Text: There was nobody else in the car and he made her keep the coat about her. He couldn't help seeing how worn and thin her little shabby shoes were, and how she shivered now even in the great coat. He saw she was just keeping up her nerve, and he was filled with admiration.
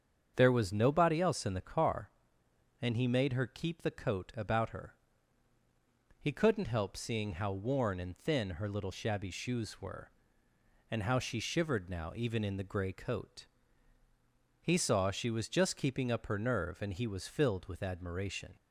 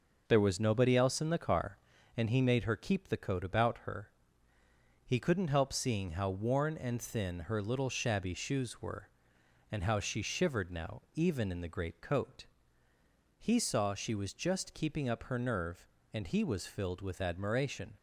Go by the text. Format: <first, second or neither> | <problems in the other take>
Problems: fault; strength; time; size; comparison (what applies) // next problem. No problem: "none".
second | starts louder than the rest; strong; until 1.3 s; 7.5 dB // says "grey" for "great"; at 12.6 s